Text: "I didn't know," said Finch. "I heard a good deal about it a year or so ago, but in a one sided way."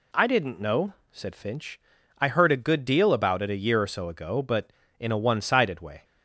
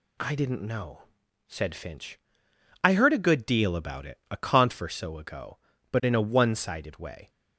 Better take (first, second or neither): first